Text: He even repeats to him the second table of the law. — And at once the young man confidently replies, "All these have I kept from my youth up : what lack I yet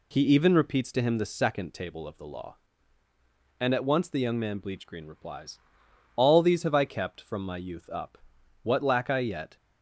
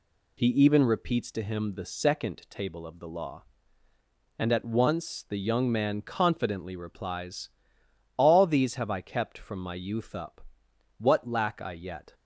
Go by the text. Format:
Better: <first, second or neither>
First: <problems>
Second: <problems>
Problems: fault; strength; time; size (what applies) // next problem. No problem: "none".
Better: second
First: says "bleachgreen" for "confidently"; at 4.5 s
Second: none